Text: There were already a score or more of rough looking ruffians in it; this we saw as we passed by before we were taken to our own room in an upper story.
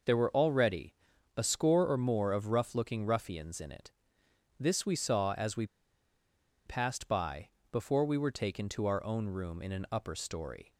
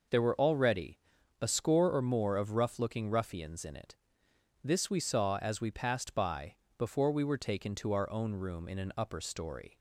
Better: second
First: pauses between "already" and "a"; at 0.9 s; 0.42 s long // pauses between "we" and "passed"; at 5.6 s; 1.0 s long // pauses between "by" and "before"; slight; at 7.4 s; 0.22 s long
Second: pauses between "already" and "a"; at 0.9 s; 0.42 s long // pauses between "by" and "before"; slight; at 6.5 s; 0.22 s long

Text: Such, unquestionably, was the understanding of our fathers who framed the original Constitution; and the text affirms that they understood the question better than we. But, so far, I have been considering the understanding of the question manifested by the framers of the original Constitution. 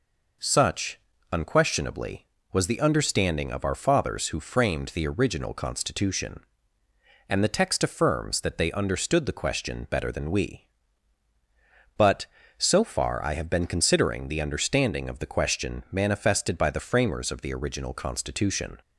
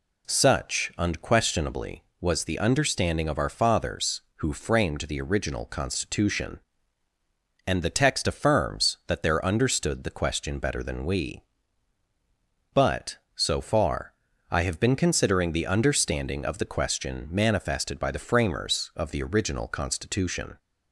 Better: first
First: none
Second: says "there" for "they"; at 9.2 s

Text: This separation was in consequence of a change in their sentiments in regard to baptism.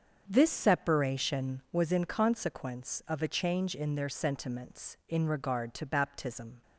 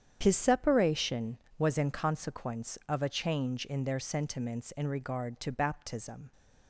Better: first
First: starts louder than the rest; until 1.2 s; 7 dB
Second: starts louder than the rest; strong; until 1.2 s; 9 dB // says "His" for "This"; at 0.2 s

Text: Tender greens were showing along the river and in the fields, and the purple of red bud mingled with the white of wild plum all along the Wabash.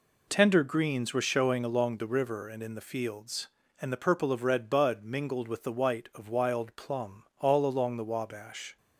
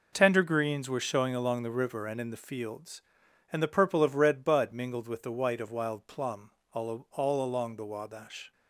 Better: first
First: pauses between "plum" and "all"; slight; at 7.2 s; 0.16 s long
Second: pauses between "plum" and "all"; slight; at 6.5 s; 0.20 s long // says "all" twice; at 7.0 s

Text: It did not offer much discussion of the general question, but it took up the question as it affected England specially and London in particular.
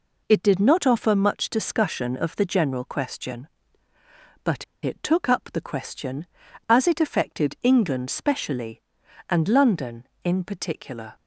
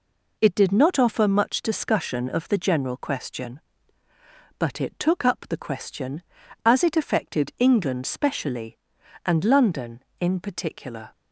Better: second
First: pauses between "but" and "it"; slight; at 4.6 s; 0.18 s long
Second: none

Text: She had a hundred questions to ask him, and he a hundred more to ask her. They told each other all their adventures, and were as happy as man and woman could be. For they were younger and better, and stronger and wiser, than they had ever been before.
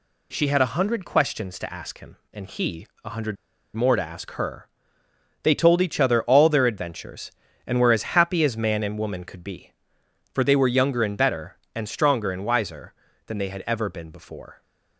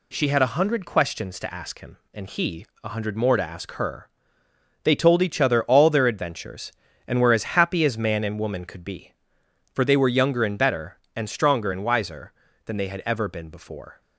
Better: second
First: pauses between "he" and "a"; slight; at 2.8 s; 0.16 s long // pauses between "hundred" and "more"; at 3.3 s; 0.40 s long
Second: pauses between "he" and "a"; slight; at 2.6 s; 0.16 s long

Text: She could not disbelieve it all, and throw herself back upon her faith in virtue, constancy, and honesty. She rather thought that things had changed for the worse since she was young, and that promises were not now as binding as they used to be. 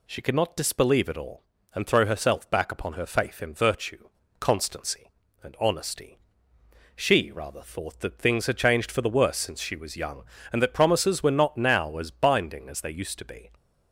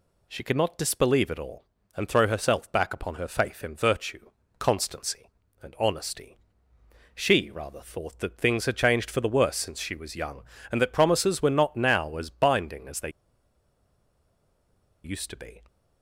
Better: first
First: none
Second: pauses between "they" and "used"; strong; at 13.0 s; 1.9 s long

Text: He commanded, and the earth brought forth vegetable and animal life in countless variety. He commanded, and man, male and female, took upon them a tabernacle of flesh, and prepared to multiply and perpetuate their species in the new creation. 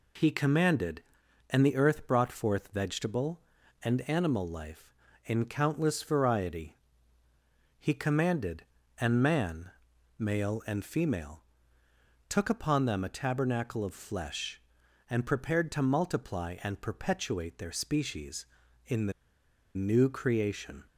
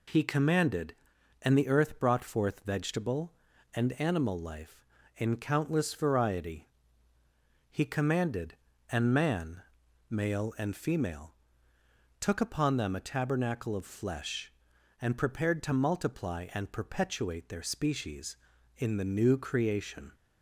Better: second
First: pauses between "the" and "new"; noticeable; at 19.1 s; 0.64 s long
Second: none

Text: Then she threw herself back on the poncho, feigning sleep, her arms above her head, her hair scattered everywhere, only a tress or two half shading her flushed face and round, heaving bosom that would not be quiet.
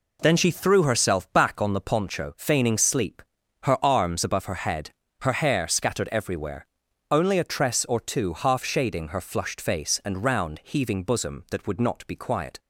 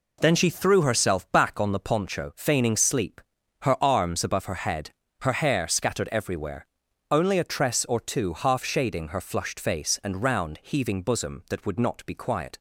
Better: neither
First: none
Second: none

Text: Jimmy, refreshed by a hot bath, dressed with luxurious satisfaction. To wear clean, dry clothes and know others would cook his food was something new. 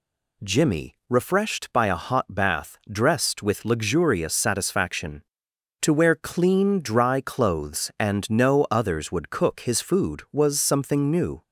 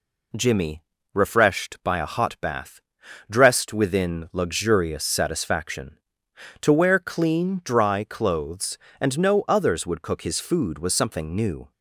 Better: first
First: none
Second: says "within" for "with"; at 3.7 s

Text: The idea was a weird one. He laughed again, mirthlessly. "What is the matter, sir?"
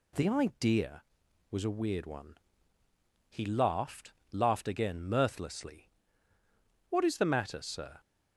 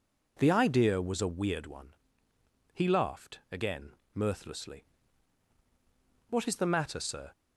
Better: second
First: says "laughed" twice; at 4.3 s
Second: none

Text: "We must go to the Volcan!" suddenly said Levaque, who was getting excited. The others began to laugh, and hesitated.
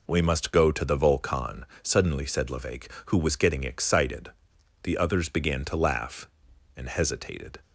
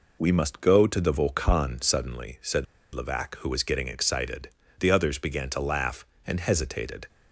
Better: first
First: none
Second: pauses between "said" and "Levaque"; slight; at 2.6 s; 0.28 s long

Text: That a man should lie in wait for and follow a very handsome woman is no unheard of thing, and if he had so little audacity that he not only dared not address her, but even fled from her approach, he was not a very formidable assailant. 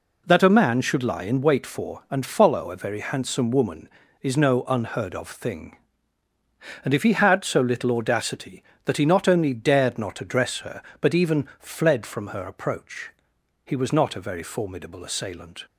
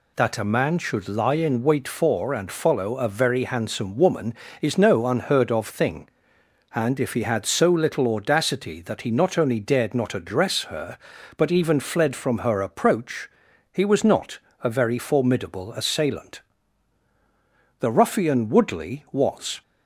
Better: first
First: none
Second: pauses between "not" and "a"; slight; at 14.3 s; 0.22 s long // goes on to say "The ruffian Woodley was"; strong; from 17.7 s on; 1.8 s long

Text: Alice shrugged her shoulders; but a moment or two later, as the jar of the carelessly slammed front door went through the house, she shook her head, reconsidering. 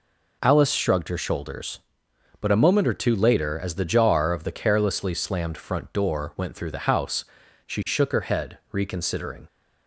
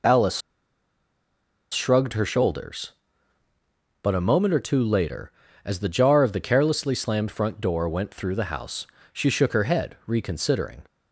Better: first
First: none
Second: pauses between "Alice" and "shrugged"; strong; at 0.4 s; 1.3 s long

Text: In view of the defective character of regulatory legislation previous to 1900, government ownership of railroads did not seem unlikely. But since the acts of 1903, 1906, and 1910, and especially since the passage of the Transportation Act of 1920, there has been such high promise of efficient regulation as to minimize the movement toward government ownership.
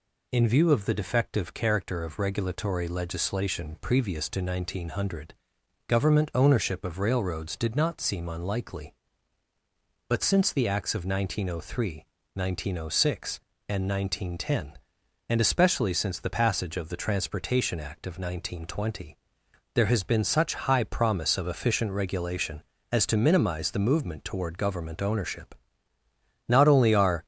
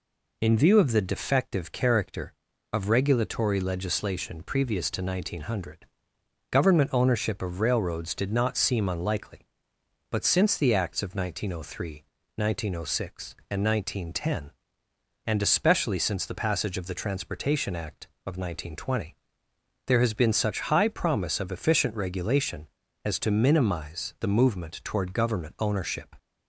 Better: second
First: goes on to say "Not only are"; noticeable; from 26.4 s on; 0.76 s long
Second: none

